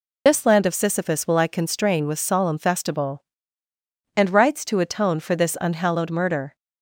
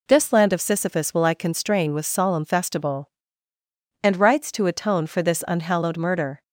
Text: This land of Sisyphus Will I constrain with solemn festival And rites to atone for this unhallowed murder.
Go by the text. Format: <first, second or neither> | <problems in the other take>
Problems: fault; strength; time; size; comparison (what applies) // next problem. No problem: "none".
second | loses the start of "This"; at 0.2 s; 45 ms